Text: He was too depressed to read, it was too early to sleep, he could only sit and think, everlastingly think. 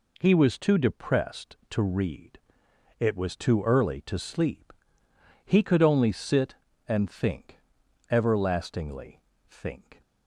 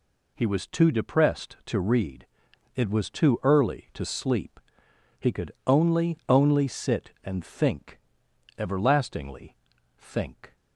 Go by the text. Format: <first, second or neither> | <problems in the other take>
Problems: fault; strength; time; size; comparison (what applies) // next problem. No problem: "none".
first | says "only" twice; at 6.2 s // pauses between "everlastingly" and "think"; at 9.5 s; 0.42 s long; slight in the first